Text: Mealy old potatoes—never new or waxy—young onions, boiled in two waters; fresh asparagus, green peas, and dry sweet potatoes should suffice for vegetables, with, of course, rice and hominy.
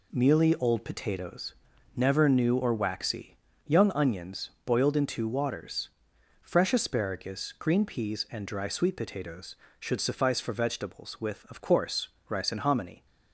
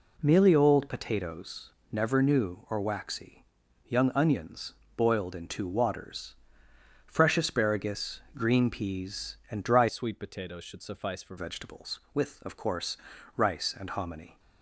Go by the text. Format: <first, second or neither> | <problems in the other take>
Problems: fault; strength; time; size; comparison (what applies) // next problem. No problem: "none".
first | changes voice from "sweet" to "for"; from 9.8 to 11.3 s; 1.5 s long